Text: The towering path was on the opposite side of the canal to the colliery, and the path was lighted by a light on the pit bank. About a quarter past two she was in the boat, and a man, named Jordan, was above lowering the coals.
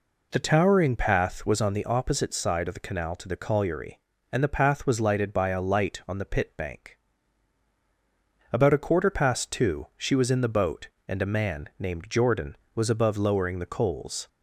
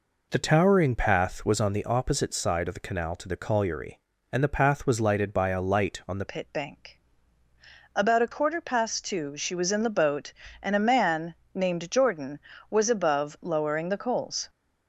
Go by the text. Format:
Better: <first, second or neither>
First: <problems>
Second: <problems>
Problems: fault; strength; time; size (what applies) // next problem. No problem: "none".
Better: first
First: none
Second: changes voice at "pit"; from 6.2 s on; 8.2 s long